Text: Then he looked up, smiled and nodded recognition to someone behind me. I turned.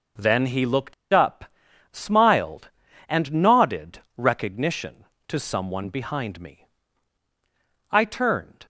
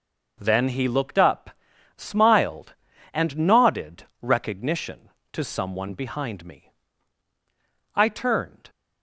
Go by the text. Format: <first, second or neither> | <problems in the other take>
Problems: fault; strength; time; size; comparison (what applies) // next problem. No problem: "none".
second | pauses between "looked" and "up"; slight; at 0.9 s; 0.19 s long // pauses between "nodded" and "recognition"; slight; at 3.9 s; 0.18 s long; slight in the second